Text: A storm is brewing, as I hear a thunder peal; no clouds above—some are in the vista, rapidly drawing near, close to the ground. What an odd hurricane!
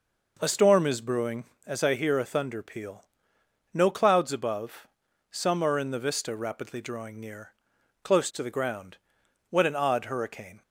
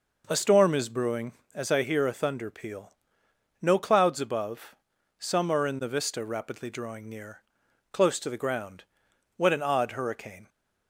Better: neither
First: none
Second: none

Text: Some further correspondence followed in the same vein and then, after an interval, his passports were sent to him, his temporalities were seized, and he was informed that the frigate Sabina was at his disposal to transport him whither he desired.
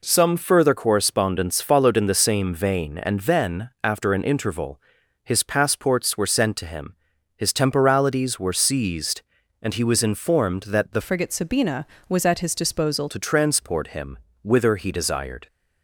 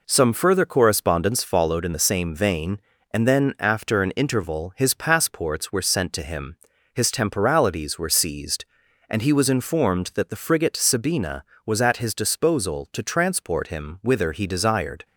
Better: second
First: changes voice from "frigate" to "disposal"; from 10.9 to 13.0 s; 2.1 s long // pauses between "him" and "whither"; slight; at 14.1 s; 0.24 s long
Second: none

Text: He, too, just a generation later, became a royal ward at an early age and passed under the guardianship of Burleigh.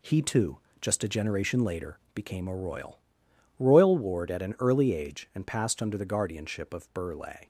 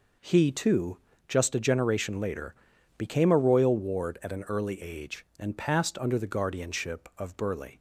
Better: second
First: says "royal" twice; at 3.5 s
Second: none

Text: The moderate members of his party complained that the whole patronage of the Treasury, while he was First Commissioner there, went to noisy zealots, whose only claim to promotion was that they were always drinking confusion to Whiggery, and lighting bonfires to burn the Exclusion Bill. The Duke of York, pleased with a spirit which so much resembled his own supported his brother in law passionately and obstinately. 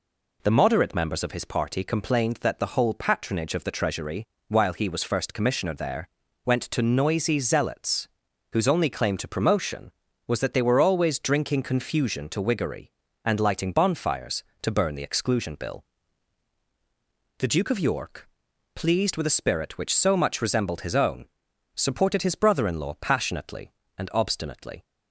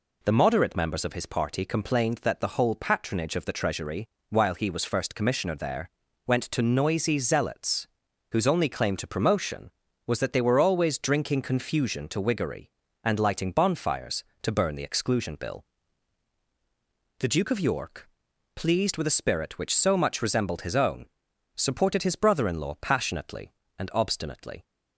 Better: neither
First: pauses between "own" and "supported"; noticeable; at 21.2 s; 0.50 s long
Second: pauses between "own" and "supported"; noticeable; at 21.0 s; 0.50 s long

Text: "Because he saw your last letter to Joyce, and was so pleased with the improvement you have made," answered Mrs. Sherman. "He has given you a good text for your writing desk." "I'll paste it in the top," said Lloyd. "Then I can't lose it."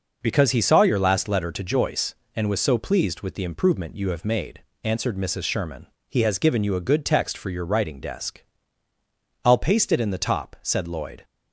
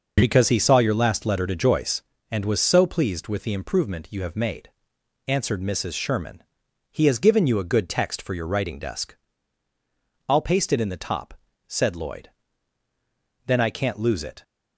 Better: second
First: stops before "Then I can't lose it"; at 11.2 s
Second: none

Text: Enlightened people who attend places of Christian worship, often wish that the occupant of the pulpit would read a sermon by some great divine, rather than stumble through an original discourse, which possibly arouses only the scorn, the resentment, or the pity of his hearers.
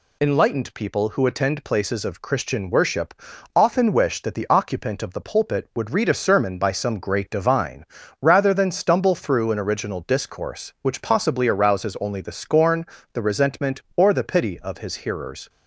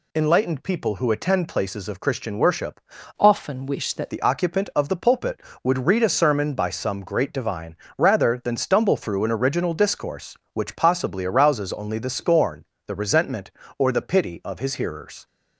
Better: first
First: none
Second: changes voice from "often" to "that"; from 3.1 to 4.1 s; 1.0 s long

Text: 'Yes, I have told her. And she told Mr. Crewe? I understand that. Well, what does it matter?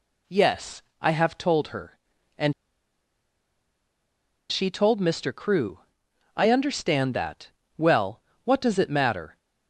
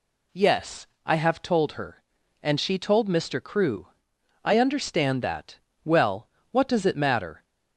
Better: second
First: pauses between "And" and "she"; strong; at 2.5 s; 1.9 s long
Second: none

